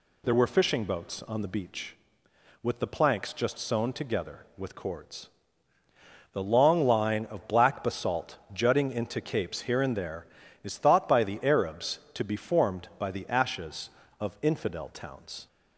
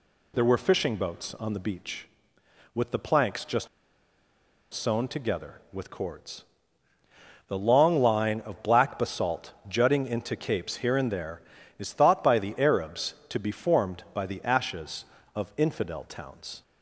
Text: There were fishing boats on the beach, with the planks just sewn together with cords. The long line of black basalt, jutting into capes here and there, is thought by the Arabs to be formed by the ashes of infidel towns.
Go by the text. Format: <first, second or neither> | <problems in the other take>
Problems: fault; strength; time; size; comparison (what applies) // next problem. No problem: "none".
first | pauses between "just" and "sewn"; at 3.6 s; 1.0 s long